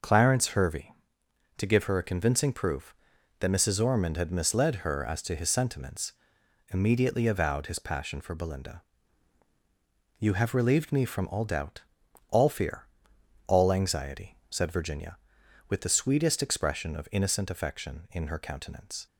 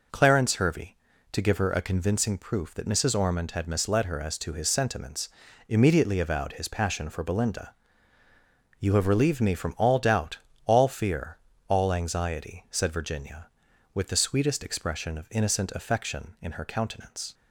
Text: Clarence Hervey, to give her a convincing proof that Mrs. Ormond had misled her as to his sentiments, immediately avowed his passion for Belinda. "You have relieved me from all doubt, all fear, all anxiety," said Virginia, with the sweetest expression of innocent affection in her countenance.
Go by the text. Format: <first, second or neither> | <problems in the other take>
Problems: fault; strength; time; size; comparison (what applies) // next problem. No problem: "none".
neither | none